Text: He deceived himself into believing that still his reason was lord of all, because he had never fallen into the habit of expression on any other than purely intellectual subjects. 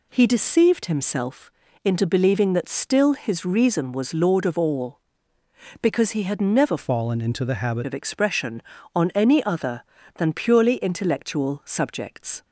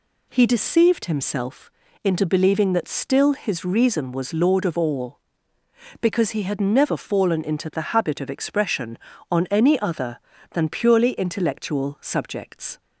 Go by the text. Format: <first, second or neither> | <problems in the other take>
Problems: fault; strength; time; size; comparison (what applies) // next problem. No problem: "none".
second | pauses between "himself" and "into"; slight; at 1.5 s; 0.34 s long; slight in the second // changes voice from "fallen" to "habit"; from 6.7 to 7.8 s; 1.1 s long